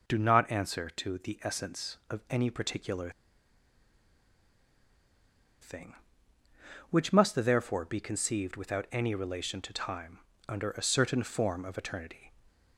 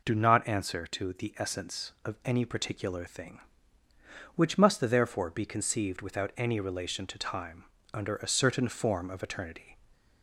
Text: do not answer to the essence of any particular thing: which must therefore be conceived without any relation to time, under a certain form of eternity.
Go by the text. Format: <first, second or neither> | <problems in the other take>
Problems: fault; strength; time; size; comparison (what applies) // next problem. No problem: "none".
second | pauses between "particular" and "thing"; strong; at 3.0 s; 2.5 s long